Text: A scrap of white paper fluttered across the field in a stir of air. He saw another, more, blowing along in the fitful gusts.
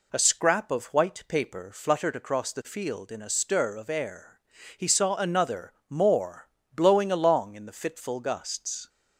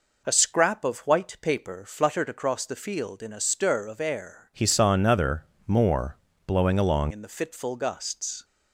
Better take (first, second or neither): first